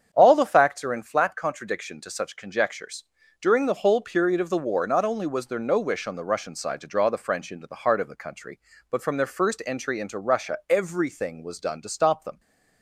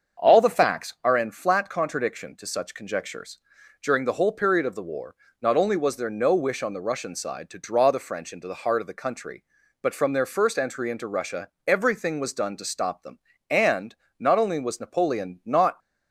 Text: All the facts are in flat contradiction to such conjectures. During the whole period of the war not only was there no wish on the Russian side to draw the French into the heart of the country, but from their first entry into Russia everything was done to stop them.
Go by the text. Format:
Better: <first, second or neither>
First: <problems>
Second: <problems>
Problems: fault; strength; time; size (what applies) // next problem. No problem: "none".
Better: first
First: starts louder than the rest; strong; until 1.1 s; 8 dB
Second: starts louder than the rest; until 1.2 s; 7 dB // pauses between "war" and "not"; slight; at 5.1 s; 0.26 s long // pauses between "Russia" and "everything"; slight; at 11.5 s; 0.18 s long // goes on to say "And not only was Napoleon not"; strong; from 13.4 s on; 2.3 s long